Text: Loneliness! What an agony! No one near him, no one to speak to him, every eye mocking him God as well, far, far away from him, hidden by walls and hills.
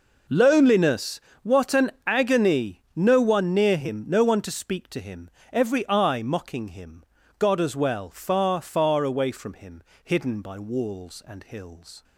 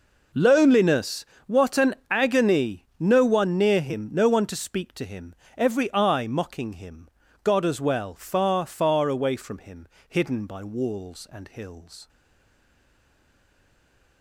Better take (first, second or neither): first